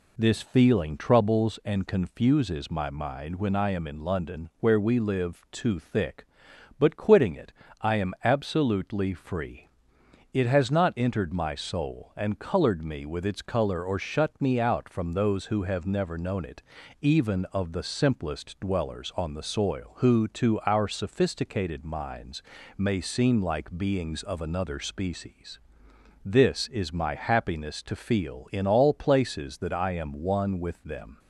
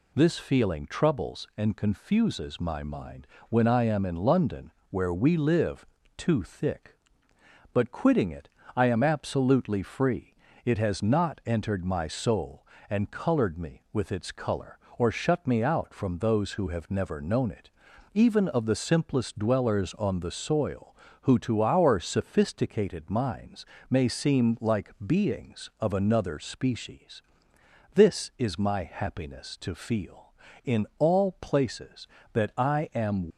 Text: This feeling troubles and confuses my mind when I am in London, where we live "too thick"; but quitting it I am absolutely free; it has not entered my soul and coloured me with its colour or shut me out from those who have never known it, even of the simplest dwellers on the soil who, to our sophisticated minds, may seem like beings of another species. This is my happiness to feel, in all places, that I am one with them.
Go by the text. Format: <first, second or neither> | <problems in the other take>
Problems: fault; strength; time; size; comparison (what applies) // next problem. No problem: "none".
first | pauses between "mind" and "when"; slight; at 3.2 s; 0.22 s long // pauses between "live" and "too"; slight; at 5.8 s; 0.32 s long // pauses between "it" and "I"; slight; at 8.4 s; 0.26 s long; slight in the first // stops before "one with them"; at 33.3 s